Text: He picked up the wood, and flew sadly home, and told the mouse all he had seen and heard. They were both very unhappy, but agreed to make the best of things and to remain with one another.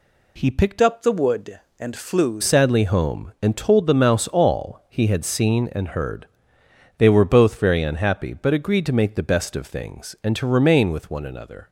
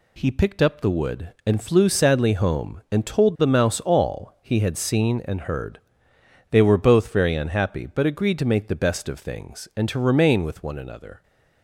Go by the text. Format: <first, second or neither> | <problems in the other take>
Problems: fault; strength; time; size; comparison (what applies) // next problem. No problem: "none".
second | changes voice from "up" to "flew"; from 0.8 to 2.4 s; 1.6 s long